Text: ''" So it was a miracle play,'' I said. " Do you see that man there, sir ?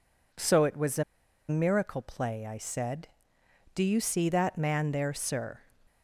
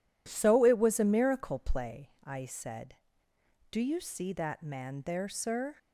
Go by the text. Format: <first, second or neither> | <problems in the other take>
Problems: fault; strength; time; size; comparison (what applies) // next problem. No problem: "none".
second | pauses between "a" and "miracle"; noticeable; at 1.0 s; 0.46 s long